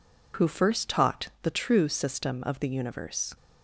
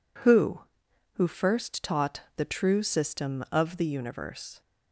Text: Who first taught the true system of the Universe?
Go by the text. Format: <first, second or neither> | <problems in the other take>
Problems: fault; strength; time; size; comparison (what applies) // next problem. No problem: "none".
first | says "Who" twice; at 1.1 s // pauses between "taught" and "the"; slight; at 2.2 s; 0.16 s long